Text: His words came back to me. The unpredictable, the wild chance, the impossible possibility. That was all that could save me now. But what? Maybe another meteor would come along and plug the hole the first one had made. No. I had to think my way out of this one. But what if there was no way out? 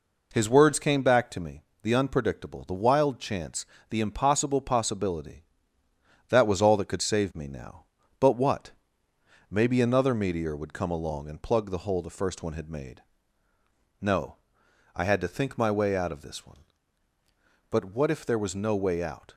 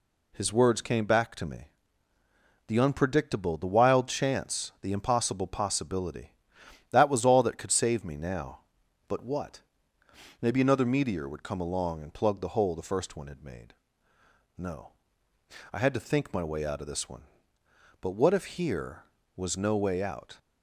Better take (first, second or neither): first